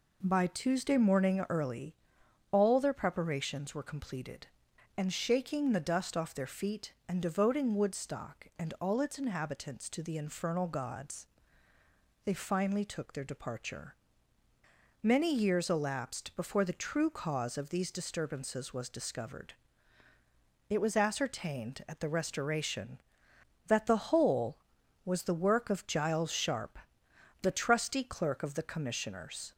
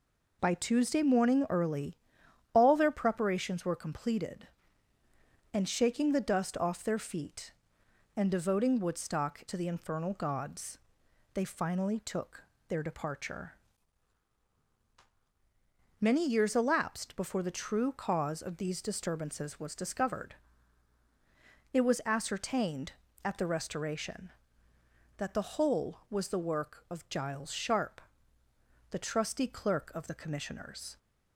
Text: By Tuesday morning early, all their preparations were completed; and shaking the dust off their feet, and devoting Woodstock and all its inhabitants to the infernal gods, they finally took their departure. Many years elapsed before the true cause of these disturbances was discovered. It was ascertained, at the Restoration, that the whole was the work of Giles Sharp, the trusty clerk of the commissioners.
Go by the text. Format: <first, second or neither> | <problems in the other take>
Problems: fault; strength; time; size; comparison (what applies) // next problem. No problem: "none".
first | skips "and all its inhabitants"; at 9.4 s // pauses between "took" and "their"; slight; at 12.4 s; 0.28 s long